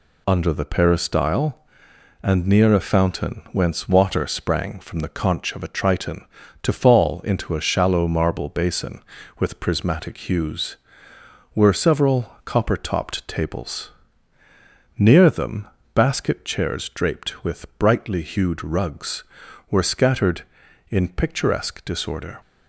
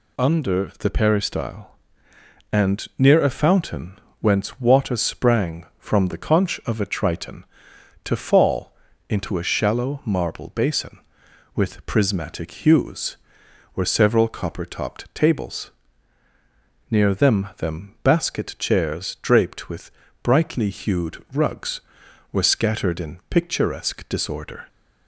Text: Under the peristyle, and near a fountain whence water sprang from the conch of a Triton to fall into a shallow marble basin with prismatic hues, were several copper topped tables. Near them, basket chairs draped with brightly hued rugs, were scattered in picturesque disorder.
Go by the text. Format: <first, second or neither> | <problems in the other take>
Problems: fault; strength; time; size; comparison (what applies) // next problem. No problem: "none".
first | pauses between "fountain" and "whence"; slight; at 3.9 s; 0.22 s long // pauses between "fall" and "into"; slight; at 8.7 s; 0.34 s long // says "them" twice; at 17.5 s // pauses between "with" and "brightly"; slight; at 19.8 s; 0.32 s long